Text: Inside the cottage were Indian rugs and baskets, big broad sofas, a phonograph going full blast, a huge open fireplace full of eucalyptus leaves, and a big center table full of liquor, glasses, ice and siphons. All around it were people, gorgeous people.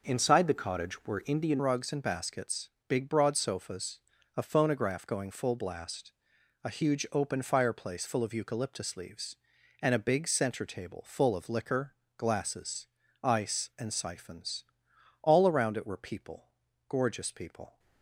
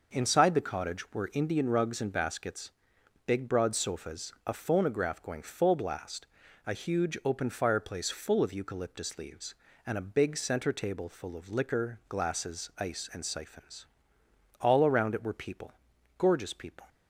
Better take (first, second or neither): second